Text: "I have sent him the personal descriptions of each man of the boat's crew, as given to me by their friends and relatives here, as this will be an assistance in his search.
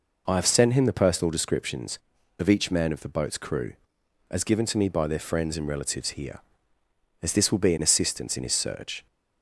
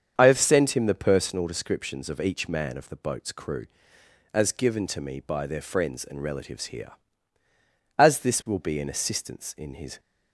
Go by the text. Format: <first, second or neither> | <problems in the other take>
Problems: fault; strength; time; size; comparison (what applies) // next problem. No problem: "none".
first | starts louder than the rest; until 1.2 s; 7 dB // stops before "search"; at 9.9 s